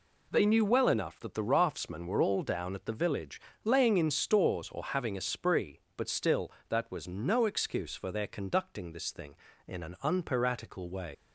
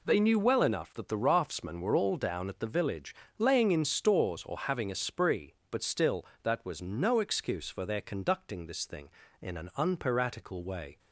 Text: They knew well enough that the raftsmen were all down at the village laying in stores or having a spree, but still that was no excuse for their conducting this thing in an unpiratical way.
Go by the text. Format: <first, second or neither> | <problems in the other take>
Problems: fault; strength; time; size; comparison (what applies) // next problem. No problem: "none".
second | pauses between "village" and "laying"; slight; at 3.4 s; 0.24 s long; slight in the second // leaves "way" unfinished; at 11.1 s; 95 ms